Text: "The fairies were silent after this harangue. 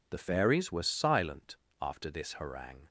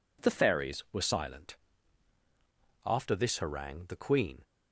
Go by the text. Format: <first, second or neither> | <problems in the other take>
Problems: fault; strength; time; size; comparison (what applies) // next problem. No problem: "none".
first | pauses between "silent" and "after"; strong; at 1.5 s; 1.2 s long; slight in the first // goes on to say "The queen"; from 3.8 s on; 0.56 s long